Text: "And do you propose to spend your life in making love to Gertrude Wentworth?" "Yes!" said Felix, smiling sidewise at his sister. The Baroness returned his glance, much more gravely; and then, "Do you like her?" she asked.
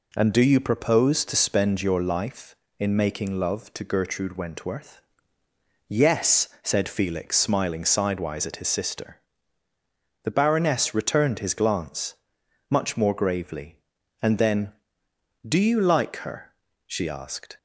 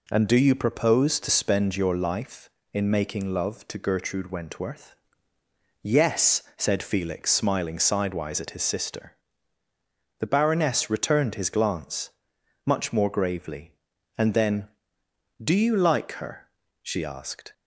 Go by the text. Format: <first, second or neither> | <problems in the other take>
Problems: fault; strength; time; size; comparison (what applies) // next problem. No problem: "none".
neither | none